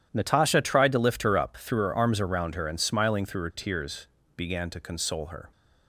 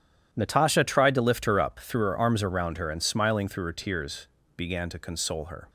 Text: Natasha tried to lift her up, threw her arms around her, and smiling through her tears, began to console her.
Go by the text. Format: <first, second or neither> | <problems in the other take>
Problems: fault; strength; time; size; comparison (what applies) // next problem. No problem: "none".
neither | starts louder than the rest; strong; the same in both